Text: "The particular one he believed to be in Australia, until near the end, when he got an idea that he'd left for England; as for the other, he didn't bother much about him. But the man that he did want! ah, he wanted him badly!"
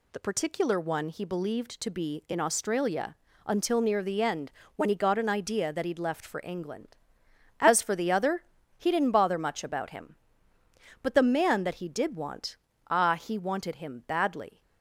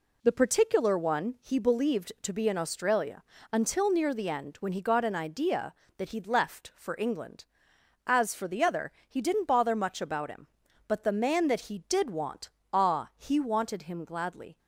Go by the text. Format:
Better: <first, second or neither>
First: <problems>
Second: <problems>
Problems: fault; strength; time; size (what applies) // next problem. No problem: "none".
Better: first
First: none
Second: says "gladly" for "badly"; at 14.0 s